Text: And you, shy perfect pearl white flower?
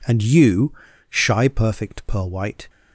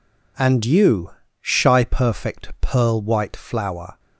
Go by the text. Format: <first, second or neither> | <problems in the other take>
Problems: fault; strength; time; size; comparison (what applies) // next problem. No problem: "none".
second | stops before "flower"; at 2.6 s